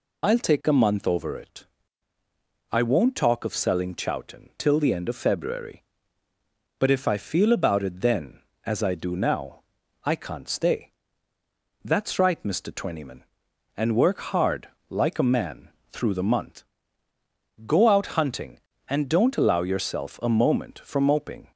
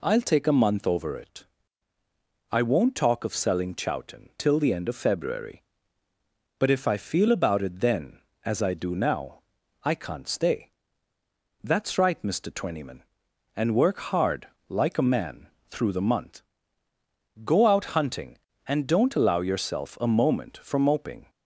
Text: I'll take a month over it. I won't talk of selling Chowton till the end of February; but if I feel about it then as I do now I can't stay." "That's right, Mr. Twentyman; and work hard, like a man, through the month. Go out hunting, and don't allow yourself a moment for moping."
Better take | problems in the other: second | loses the start of "I'll"; at 0.2 s; 40 ms // pauses between "now" and "I"; at 9.6 s; 0.40 s long; also in the second

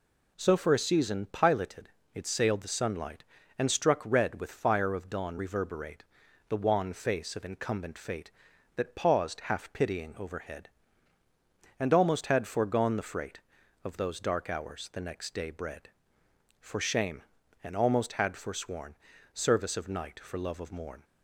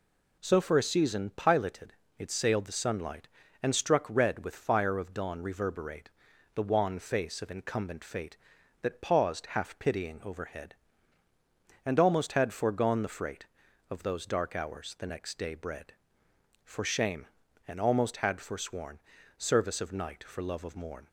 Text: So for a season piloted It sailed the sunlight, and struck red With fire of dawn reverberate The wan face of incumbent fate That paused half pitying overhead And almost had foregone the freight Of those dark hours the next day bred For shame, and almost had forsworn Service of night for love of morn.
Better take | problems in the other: neither | pauses between "piloted" and "It"; slight; the same in both // pauses between "reverberate" and "The"; the same in both // pauses between "forsworn" and "Service"; the same in both

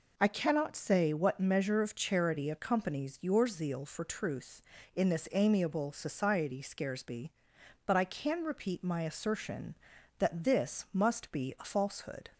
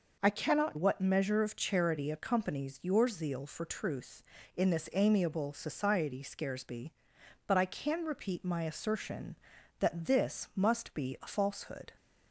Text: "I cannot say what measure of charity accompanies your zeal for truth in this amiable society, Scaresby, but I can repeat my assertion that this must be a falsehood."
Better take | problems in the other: first | skips "say"; at 0.7 s

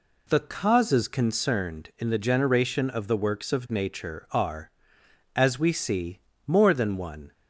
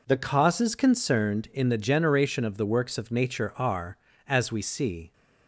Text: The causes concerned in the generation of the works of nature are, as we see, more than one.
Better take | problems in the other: first | stops before "more than one"; at 5.1 s

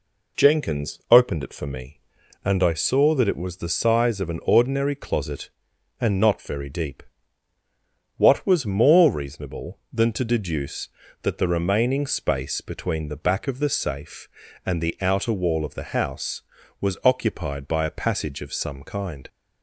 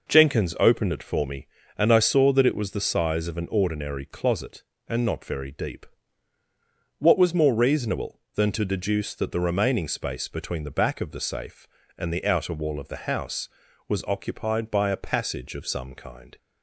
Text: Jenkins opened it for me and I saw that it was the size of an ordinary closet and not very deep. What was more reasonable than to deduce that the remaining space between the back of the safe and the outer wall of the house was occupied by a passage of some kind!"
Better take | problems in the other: neither | none

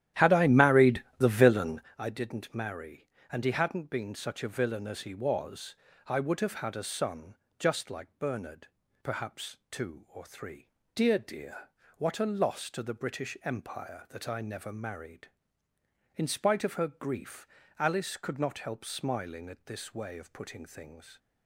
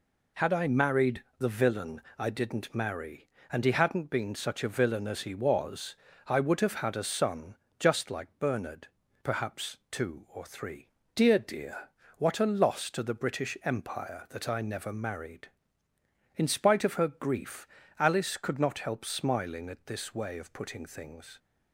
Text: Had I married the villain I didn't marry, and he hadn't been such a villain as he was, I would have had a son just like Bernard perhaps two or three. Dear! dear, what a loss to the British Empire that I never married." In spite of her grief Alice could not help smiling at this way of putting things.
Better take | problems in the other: second | starts louder than the rest; strong; until 1.9 s; 12 dB // pauses between "married" and "the"; slight; at 1.0 s; 0.16 s long; slight in the second // pauses between "villain" and "I"; slight; at 1.8 s; 0.18 s long; slight in the second // pauses between "son" and "just"; slight; at 7.3 s; 0.24 s long; slight in the second // pauses between "Bernard" and "perhaps"; slight; at 8.6 s; 0.34 s long; slight in the second // pauses between "grief" and "Alice"; slight; at 17.4 s; 0.32 s long; slight in the second

